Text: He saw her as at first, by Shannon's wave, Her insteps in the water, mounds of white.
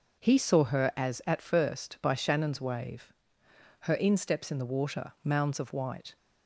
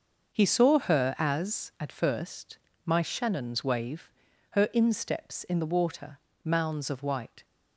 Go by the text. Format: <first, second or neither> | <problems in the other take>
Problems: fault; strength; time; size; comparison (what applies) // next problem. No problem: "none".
first | starts louder than the rest; until 1.3 s; 6.5 dB; noticeable in the first // says "my" for "by"; at 2.8 s